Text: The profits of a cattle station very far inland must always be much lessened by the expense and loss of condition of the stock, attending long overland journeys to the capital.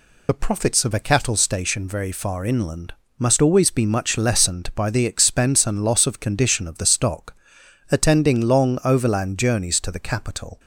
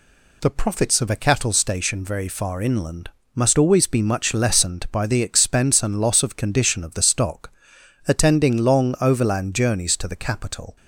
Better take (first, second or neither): second